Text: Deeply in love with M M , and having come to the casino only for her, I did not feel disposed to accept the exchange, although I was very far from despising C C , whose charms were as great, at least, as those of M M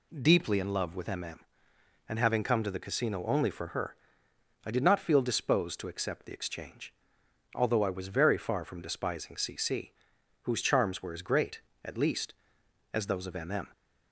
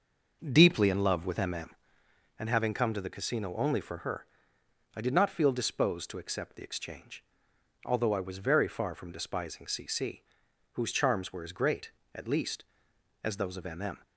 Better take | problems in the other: first | starts louder than the rest; noticeable; until 2.0 s; 6 dB

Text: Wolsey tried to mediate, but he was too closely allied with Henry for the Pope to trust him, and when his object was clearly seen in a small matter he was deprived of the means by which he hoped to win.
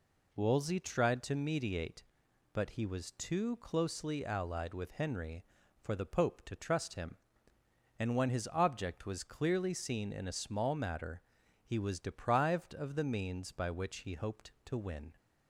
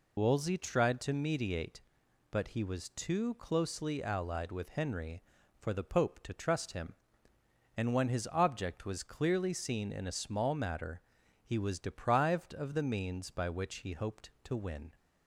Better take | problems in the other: first | loses the start of "Wolsey"; at 0.1 s; 60 ms // pauses between "matter" and "he"; at 11.0 s; 0.42 s long; also in the first

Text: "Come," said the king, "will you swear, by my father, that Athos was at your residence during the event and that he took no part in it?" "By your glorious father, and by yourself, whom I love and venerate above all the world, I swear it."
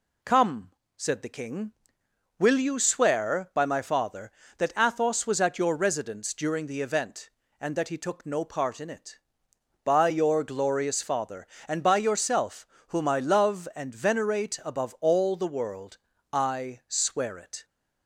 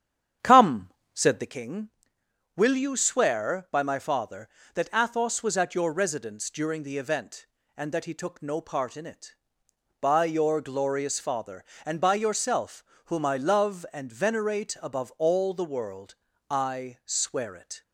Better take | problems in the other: first | starts louder than the rest; strong; until 1.6 s; 9 dB

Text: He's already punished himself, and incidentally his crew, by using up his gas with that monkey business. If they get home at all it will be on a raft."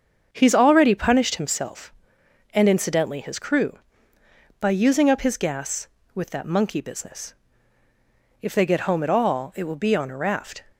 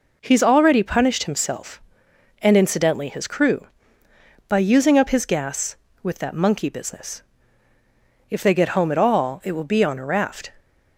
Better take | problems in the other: second | starts louder than the rest; until 1.6 s; 7 dB

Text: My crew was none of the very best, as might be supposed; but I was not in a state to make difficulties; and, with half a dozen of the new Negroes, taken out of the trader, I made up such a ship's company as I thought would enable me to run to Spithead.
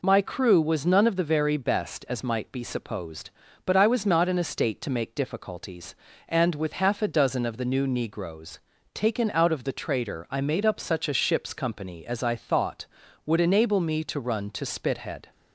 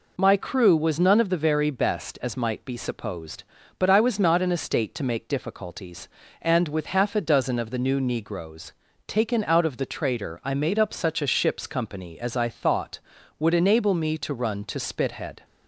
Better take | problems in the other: neither | none

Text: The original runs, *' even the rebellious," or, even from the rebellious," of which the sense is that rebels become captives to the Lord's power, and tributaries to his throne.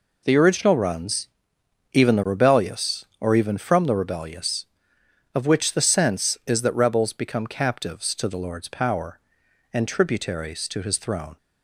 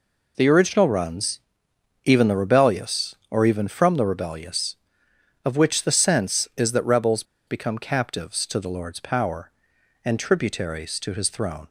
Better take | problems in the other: first | pauses between "rebels" and "become"; slight; at 7.2 s; 0.24 s long

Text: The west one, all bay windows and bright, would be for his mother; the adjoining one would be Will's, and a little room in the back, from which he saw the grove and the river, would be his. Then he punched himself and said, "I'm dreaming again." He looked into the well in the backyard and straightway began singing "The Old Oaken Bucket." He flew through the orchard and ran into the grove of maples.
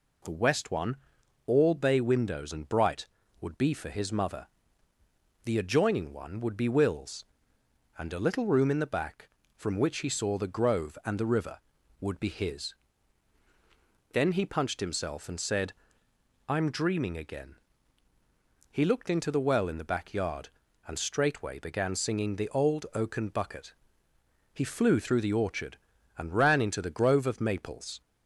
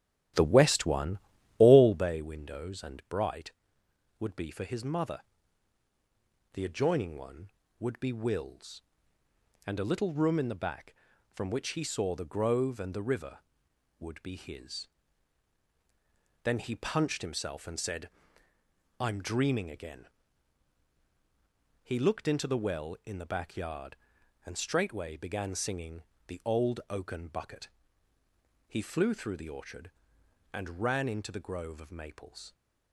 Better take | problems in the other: first | starts louder than the rest; strong; until 2.1 s; 12.5 dB // pauses between "singing" and "The"; slight; at 26.0 s; 0.24 s long

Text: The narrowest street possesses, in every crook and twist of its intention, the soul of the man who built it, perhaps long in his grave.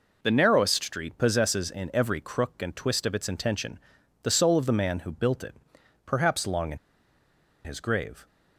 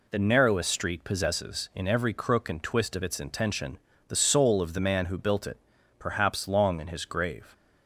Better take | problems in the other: second | pauses between "in" and "his"; noticeable; at 6.7 s; 0.87 s long

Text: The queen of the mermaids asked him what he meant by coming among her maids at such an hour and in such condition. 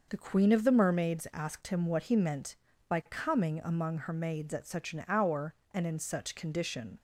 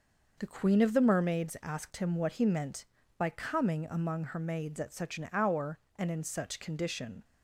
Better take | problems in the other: neither | none

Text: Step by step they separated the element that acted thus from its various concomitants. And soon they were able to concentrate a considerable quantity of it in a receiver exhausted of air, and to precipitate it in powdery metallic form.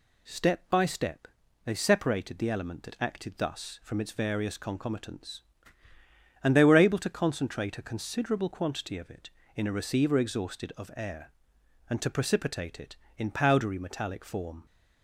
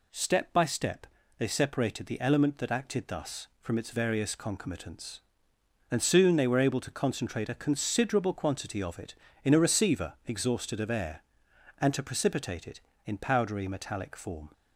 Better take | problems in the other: second | pauses between "step" and "they"; at 1.2 s; 0.38 s long; slight in the second // skips "soon"; at 6.5 s

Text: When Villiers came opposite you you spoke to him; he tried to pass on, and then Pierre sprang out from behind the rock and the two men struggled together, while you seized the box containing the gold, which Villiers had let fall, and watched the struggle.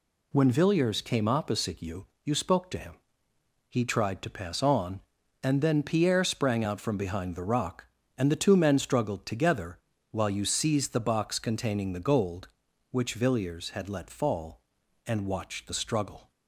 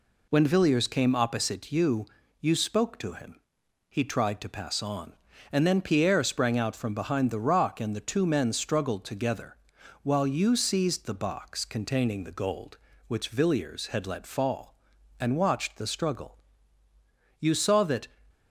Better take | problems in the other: first | pauses between "you" and "you"; slight; at 2.0 s; 0.34 s long; slight in the first // goes on to say "You saw that"; noticeable; from 17.3 s on; 0.70 s long

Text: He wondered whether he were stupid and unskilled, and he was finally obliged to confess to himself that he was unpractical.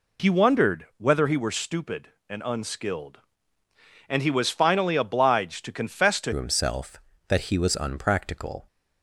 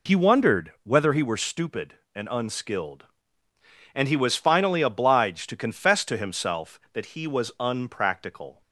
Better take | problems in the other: second | changes voice at "himself"; from 6.3 s on; 2.3 s long

